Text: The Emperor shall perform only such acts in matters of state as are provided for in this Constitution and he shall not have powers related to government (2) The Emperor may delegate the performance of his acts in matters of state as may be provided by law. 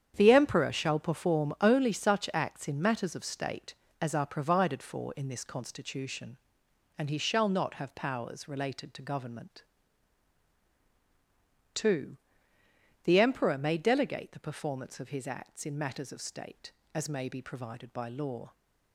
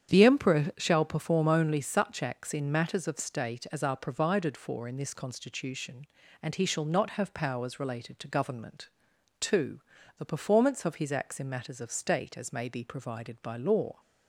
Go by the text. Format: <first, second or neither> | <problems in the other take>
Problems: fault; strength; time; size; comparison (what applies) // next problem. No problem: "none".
first | starts louder than the rest; strong; until 1.1 s; 8.5 dB; strong in the first // skips "The Emperor may delegate"; at 9.9 s